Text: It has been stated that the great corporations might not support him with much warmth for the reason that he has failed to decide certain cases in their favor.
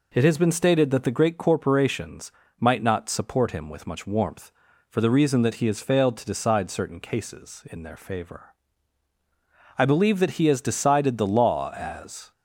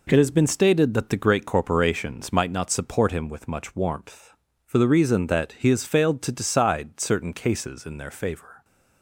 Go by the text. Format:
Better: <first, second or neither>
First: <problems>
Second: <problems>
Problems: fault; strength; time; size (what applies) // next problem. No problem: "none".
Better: second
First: pauses between "corporations" and "might"; slight; at 2.3 s; 0.28 s long // goes on to say "I believe that he has decided the law as"; strong; from 9.7 s on; 2.5 s long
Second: none